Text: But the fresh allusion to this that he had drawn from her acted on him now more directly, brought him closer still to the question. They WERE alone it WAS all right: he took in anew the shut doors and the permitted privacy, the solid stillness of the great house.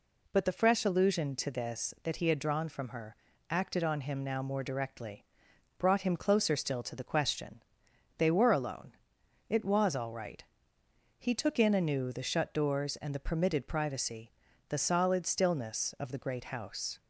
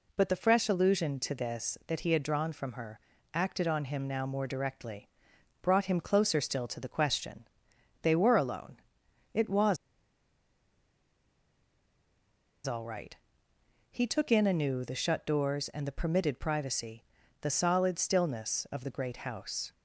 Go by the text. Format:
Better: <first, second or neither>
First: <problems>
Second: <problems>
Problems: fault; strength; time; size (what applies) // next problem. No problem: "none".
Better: first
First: pauses between "her" and "acted"; slight; at 3.1 s; 0.34 s long // pauses between "alone" and "it"; noticeable; at 8.9 s; 0.56 s long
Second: pauses between "her" and "acted"; slight; at 2.9 s; 0.34 s long // pauses between "alone" and "it"; noticeable; at 8.7 s; 0.56 s long // pauses between "WAS" and "all"; strong; at 9.7 s; 2.8 s long